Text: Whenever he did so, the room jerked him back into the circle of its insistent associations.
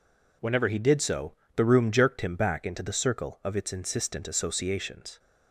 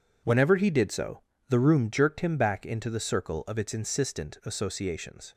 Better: first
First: none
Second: gets quieter; strong; throughout; 11 dB

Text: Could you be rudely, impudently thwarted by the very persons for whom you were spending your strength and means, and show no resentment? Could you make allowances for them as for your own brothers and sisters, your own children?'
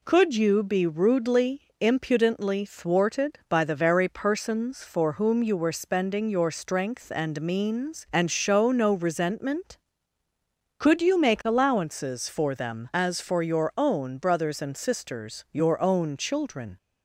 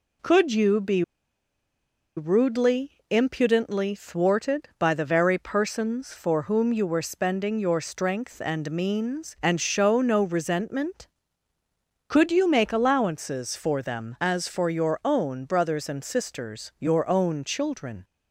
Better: first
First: none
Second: pauses between "be" and "rudely"; at 1.0 s; 1.1 s long

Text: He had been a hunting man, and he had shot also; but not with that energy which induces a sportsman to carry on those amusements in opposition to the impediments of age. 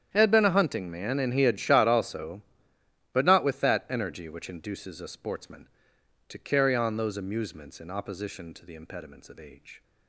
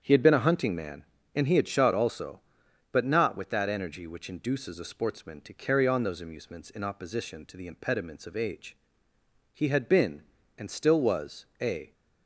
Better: first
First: starts louder than the rest; strong; until 1.1 s; 9.5 dB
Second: starts louder than the rest; strong; until 1.0 s; 8.5 dB // goes on to say "He had been and still was a"; strong; from 9.5 s on; 2.4 s long

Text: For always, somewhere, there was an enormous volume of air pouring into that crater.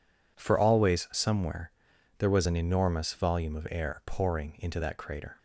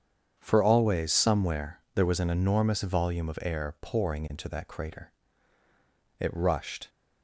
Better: first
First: none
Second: starts louder than the rest; strong; until 1.4 s; 8 dB // goes on to say "It rushed"; noticeable; from 6.1 s on; 0.70 s long

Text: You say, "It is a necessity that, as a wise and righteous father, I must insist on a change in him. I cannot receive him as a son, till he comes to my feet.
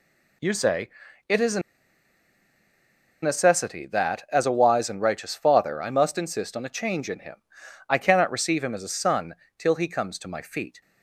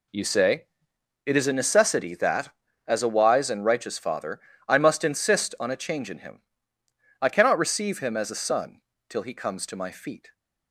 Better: second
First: pauses between "a" and "necessity"; strong; at 1.5 s; 1.6 s long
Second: none

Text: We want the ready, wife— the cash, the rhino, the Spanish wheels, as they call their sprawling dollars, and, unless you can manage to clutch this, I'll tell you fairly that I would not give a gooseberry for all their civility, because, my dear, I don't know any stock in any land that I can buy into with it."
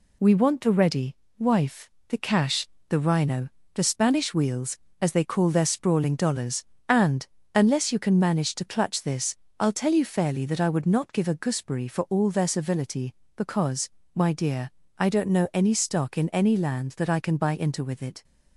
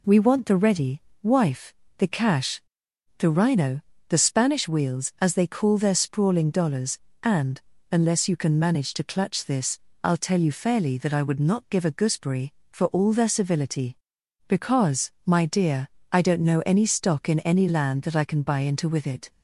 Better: second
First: gets quieter; throughout; 4 dB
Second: none

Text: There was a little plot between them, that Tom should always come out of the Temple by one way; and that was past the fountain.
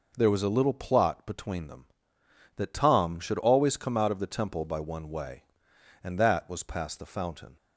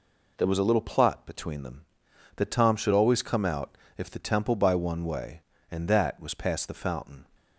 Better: first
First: none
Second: says "if" for "of"; at 3.9 s

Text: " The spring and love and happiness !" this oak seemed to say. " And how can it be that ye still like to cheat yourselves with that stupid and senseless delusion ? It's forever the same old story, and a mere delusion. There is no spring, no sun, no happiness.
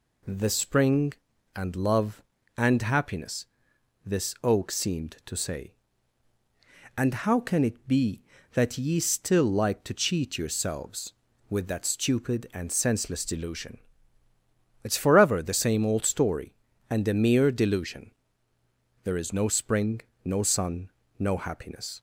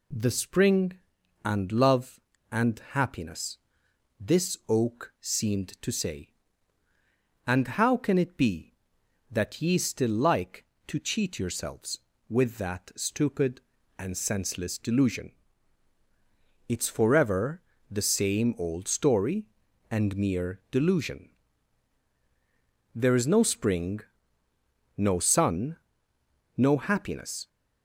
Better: first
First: none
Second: pauses between "forever" and "the"; slight; at 17.6 s; 0.28 s long // skips "a"; at 20.1 s

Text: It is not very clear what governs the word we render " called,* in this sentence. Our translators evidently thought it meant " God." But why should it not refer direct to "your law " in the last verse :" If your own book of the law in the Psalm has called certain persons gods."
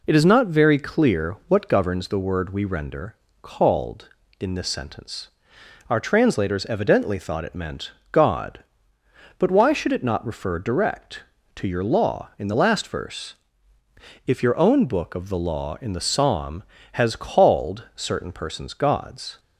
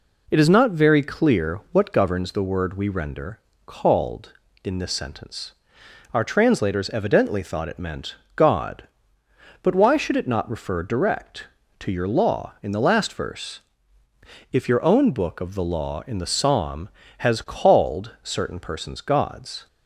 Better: neither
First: none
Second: none

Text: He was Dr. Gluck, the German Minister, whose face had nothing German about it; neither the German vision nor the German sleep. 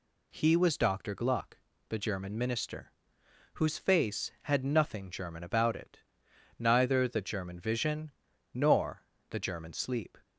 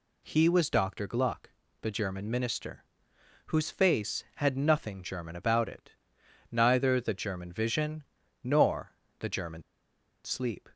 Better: first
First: pauses between "vision" and "nor"; at 8.1 s; 0.40 s long // pauses between "nor" and "the"; slight; at 9.0 s; 0.24 s long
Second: pauses between "vision" and "nor"; at 8.0 s; 0.38 s long // pauses between "nor" and "the"; slight; at 8.9 s; 0.24 s long // pauses between "German" and "sleep"; noticeable; at 9.6 s; 0.62 s long

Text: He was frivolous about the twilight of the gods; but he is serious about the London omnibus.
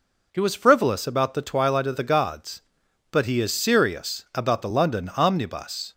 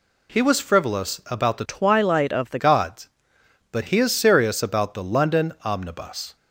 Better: first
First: none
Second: changes voice from "twilight" to "the"; from 1.6 to 2.5 s; 0.9 s long

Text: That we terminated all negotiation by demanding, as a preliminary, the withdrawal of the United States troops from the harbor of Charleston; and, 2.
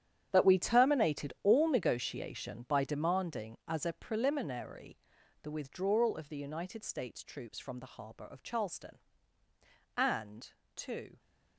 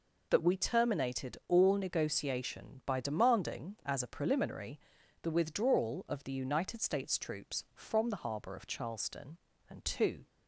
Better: second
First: gets quieter; strong; throughout; 15.5 dB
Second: none

